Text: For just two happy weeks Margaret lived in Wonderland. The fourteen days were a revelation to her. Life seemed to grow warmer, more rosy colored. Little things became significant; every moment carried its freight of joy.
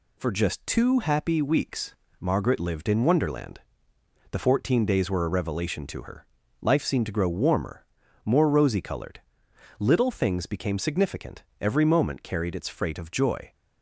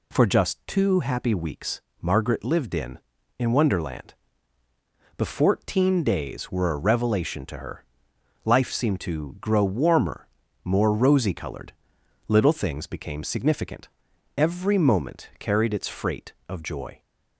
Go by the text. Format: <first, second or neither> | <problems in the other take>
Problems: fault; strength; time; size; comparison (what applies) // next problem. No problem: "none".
first | pauses between "weeks" and "Margaret"; slight; at 1.7 s; 0.22 s long; slight in the first // says "in" twice; at 3.3 s